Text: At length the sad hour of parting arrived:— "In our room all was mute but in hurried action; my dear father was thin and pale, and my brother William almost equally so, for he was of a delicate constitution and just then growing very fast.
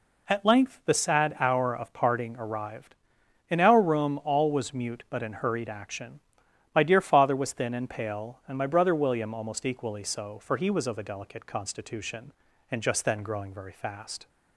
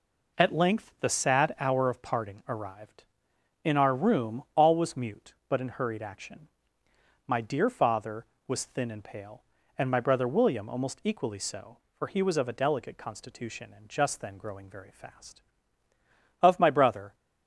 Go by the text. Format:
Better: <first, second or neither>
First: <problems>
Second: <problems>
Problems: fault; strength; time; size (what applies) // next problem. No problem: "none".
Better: first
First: none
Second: goes on to say "Of my brother"; noticeable; from 16.4 s on; 0.72 s long